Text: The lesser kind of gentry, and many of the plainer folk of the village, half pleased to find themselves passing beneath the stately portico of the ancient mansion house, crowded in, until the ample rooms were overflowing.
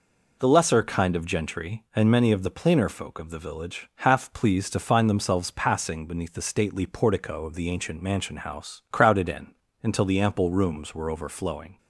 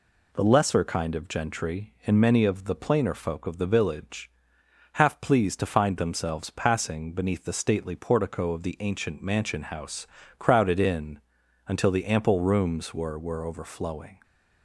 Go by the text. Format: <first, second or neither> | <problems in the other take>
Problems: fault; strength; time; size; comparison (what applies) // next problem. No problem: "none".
first | says "were" twice; at 13.1 s